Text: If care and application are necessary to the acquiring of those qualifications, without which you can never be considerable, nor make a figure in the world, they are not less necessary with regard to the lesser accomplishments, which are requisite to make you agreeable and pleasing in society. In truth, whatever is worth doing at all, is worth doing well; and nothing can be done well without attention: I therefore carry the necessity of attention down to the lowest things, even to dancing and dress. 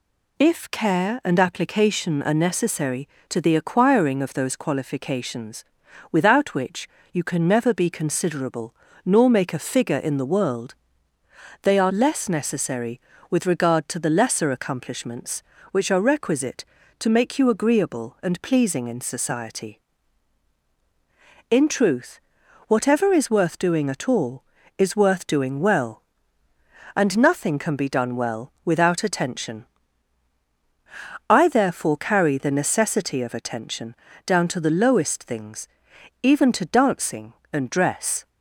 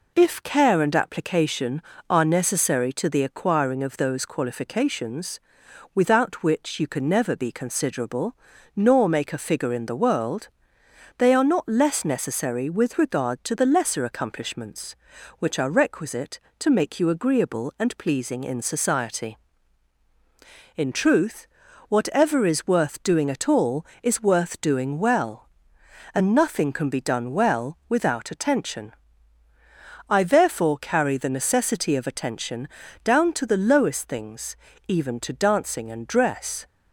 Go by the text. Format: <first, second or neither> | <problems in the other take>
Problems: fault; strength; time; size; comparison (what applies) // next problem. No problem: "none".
second | pauses between "which" and "you"; slight; at 6.8 s; 0.24 s long // skips "not"; at 11.9 s // pauses between "attention" and "down"; slight; at 33.9 s; 0.32 s long; slight in the second